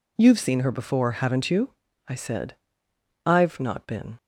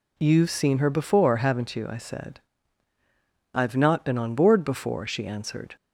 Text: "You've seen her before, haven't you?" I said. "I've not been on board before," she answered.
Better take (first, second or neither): second